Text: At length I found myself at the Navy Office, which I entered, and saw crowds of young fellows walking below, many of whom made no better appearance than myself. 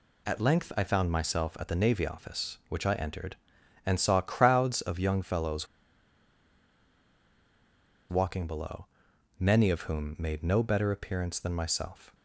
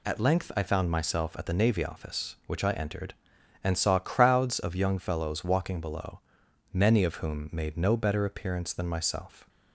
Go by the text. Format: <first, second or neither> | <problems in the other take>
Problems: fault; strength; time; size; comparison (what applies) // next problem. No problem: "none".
second | pauses between "fellows" and "walking"; strong; at 5.6 s; 2.4 s long